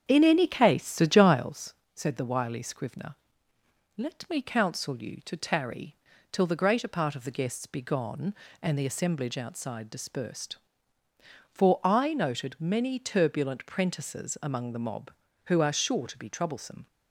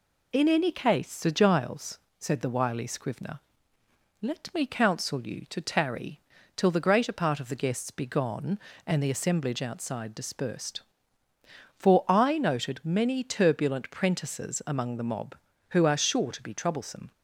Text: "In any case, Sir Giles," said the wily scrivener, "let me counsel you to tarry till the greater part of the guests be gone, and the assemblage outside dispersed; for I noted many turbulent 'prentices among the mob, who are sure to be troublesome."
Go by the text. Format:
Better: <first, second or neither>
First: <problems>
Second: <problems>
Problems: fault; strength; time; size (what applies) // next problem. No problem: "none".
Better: second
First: starts louder than the rest; strong; until 1.6 s; 8 dB // pauses between "tarry" and "till"; slight; at 5.9 s; 0.36 s long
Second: pauses between "tarry" and "till"; slight; at 6.2 s; 0.36 s long